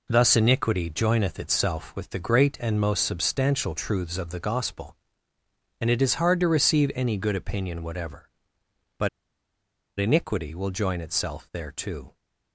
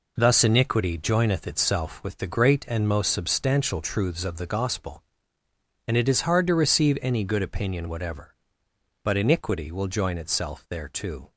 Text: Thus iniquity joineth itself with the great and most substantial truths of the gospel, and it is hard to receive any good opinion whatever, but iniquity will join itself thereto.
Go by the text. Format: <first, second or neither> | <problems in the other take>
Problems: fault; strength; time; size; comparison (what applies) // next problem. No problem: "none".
second | pauses between "but" and "iniquity"; noticeable; at 9.0 s; 0.91 s long